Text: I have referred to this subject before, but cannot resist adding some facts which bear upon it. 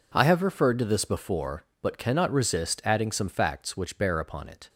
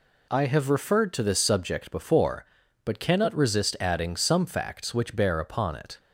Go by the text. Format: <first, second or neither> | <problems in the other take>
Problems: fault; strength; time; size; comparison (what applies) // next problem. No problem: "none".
second | skips "subject"; at 1.0 s